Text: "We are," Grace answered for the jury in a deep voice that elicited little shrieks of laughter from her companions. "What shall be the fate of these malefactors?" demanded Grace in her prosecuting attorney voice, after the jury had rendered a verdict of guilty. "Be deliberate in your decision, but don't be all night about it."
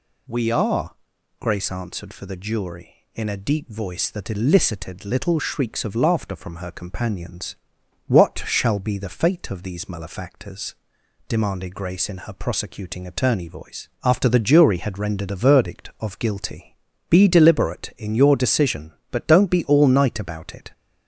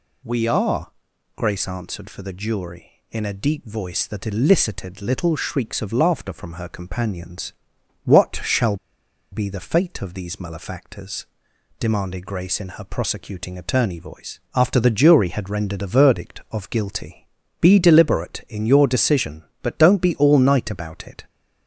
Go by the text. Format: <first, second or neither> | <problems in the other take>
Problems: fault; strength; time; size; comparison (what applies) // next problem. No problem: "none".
first | pauses between "shall" and "be"; noticeable; at 8.7 s; 0.55 s long